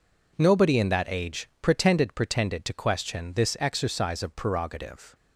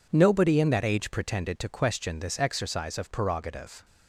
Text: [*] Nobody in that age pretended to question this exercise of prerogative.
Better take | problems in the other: second | says "pretended" twice; at 2.1 s

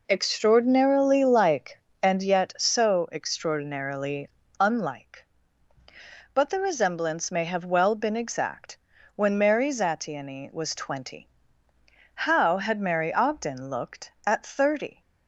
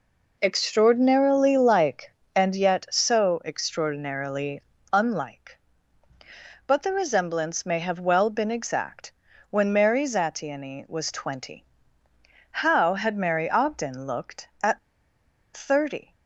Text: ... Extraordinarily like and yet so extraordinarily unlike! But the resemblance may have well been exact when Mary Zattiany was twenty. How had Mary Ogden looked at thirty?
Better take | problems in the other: first | pauses between "extraordinarily" and "unlike"; slight; at 4.6 s; 0.32 s long; slight in the first // pauses between "exact" and "when"; at 9.1 s; 0.40 s long; also in the first // pauses between "at" and "thirty"; noticeable; at 14.7 s; 0.76 s long

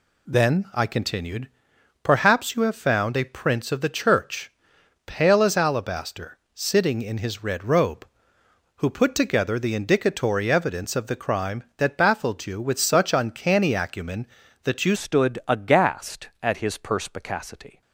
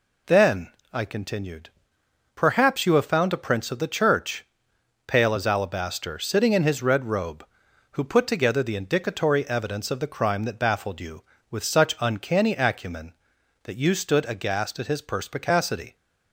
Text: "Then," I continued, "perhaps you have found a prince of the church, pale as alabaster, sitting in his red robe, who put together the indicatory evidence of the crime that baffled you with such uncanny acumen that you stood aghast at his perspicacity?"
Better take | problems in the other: second | changes voice at "stood"; from 14.9 s on; 2.9 s long

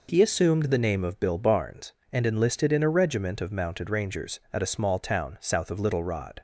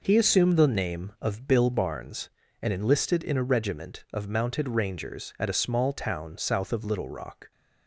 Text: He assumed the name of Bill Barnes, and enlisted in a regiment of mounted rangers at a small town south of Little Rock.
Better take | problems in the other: second | says "Rod" for "Rock"; at 6.0 s

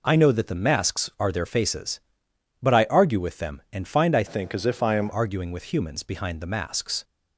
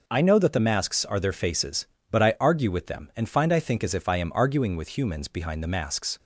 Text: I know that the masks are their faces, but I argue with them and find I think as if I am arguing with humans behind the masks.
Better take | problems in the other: second | changes voice from "think" to "am"; from 4.2 to 5.0 s; 0.8 s long

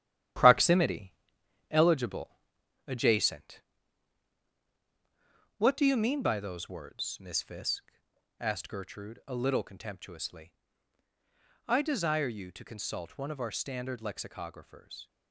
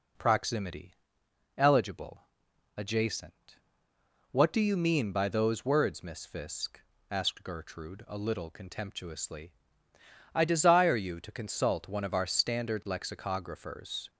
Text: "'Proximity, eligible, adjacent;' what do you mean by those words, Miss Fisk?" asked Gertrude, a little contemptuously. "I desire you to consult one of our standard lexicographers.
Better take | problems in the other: second | gets quieter; throughout; 6.5 dB

